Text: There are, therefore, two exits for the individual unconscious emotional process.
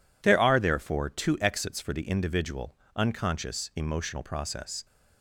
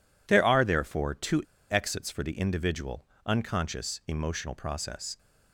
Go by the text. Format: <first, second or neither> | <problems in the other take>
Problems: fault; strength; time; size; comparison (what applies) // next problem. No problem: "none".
first | pauses between "two" and "exits"; slight; at 1.4 s; 0.27 s long // pauses between "individual" and "unconscious"; slight; at 3.0 s; 0.20 s long; slight in the first